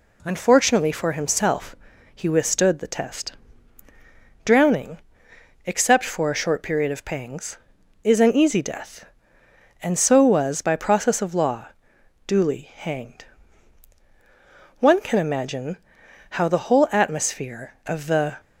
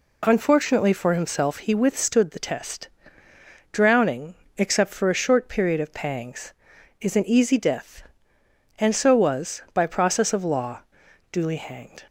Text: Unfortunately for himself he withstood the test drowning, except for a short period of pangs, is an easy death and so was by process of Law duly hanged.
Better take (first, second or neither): second